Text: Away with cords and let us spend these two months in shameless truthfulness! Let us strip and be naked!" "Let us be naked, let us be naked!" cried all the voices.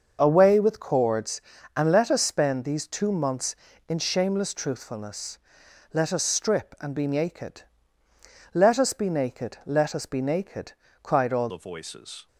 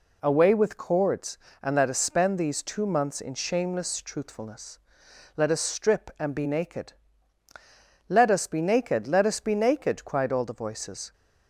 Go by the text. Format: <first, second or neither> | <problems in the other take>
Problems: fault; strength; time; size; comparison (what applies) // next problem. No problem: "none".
second | starts louder than the rest; until 1.2 s; 6.5 dB // changes voice at "the"; from 11.4 s on; 0.8 s long